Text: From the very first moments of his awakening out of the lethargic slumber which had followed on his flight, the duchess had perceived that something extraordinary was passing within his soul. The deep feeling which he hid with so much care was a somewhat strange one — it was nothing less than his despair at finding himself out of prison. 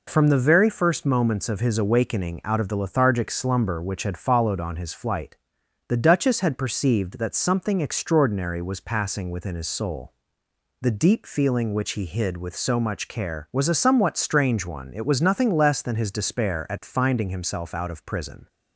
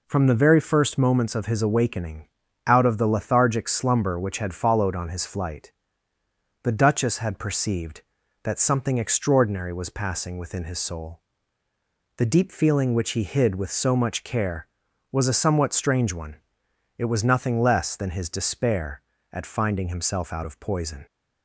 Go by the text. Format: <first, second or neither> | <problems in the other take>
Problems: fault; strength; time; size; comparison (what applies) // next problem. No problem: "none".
first | pauses between "awakening" and "out"; at 2.2 s; 0.40 s long // says "poison" for "prison"; at 20.5 s